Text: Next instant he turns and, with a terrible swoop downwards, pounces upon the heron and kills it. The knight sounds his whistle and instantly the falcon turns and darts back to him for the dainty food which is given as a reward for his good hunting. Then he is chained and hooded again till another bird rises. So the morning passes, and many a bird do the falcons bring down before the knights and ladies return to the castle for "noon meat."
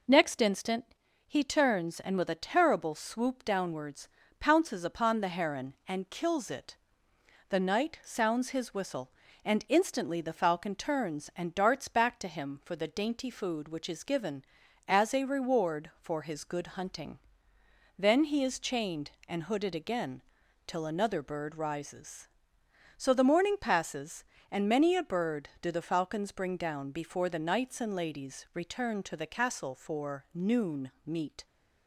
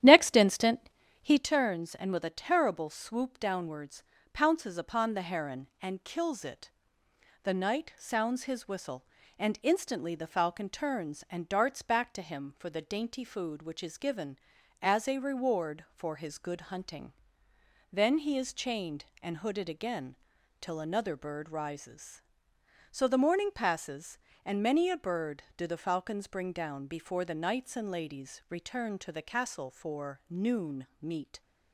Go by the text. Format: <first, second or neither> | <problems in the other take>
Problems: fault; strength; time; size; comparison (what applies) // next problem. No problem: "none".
first | starts louder than the rest; strong; until 1.5 s; 11.5 dB // pauses between "instant" and "he"; slight; at 0.8 s; 0.34 s long; slight in the first // pauses between "again" and "till"; noticeable; at 20.1 s; 0.46 s long; noticeable in the first